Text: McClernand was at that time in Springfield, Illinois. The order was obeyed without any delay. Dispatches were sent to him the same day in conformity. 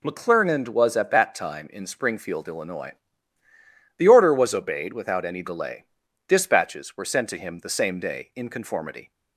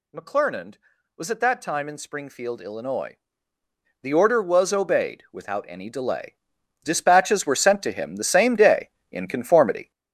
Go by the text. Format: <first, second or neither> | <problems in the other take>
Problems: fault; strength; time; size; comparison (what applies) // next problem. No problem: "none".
first | gets louder; throughout; 6.5 dB